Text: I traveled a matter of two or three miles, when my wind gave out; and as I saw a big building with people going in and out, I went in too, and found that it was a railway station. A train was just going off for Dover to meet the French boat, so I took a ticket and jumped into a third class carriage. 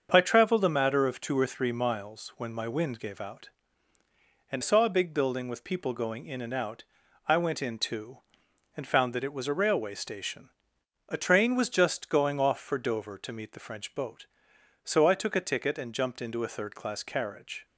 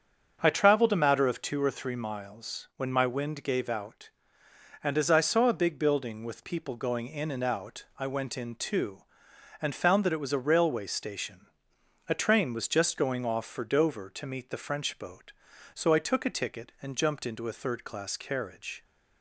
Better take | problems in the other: second | starts louder than the rest; until 1.1 s; 7 dB; also in the second // skips "as I"; at 4.6 s

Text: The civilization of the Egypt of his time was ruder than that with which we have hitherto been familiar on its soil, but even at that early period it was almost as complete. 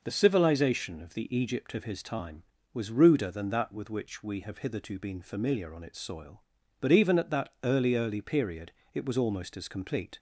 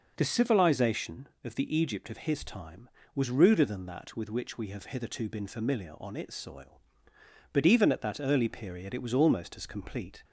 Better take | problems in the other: second | says "early" twice; at 7.9 s // pauses between "period" and "it"; slight; at 8.7 s; 0.22 s long

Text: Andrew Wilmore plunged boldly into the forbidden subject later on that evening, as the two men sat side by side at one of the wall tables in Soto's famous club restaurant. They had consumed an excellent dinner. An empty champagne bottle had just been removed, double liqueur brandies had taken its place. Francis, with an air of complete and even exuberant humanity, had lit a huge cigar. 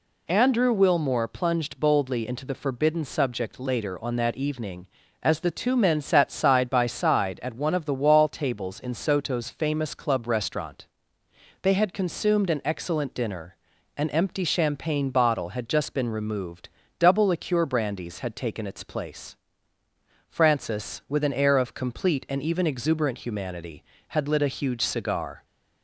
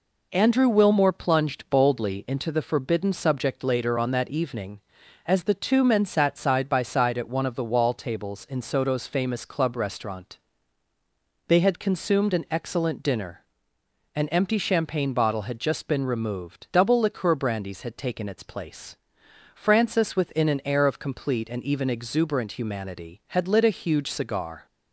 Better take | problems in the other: first | says "within" for "with"; at 20.1 s

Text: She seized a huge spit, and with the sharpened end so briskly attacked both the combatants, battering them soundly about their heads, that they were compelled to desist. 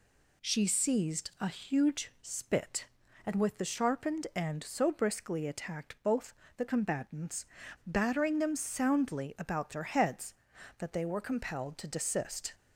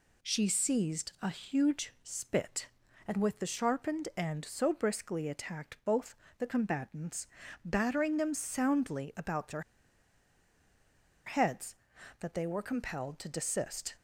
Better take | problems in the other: first | pauses between "both" and "the"; slight; at 6.1 s; 0.24 s long; slight in the first // pauses between "their" and "heads"; strong; at 9.6 s; 1.6 s long

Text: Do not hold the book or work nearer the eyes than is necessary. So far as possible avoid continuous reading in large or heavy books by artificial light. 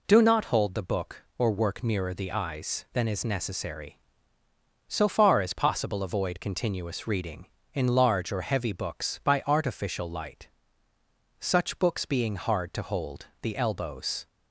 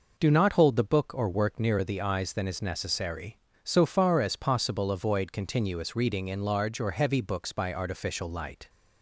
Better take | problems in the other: second | goes on to say "Such books being hard to hold the elbows"; strong; from 11.3 s on; 2.8 s long

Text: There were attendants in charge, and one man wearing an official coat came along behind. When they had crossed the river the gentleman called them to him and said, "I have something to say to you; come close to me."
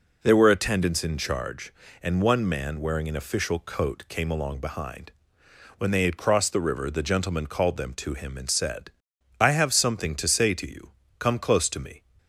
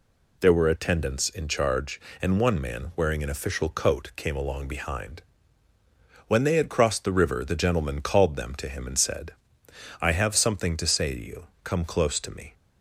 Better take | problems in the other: neither | none

